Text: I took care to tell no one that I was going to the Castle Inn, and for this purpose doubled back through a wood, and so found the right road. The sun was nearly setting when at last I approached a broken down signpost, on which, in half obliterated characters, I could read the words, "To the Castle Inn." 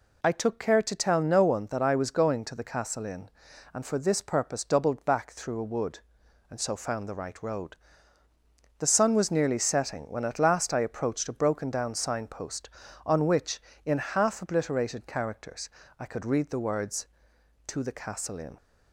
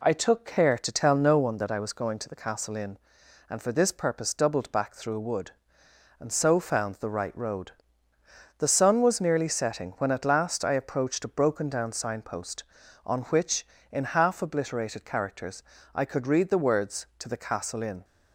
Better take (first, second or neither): neither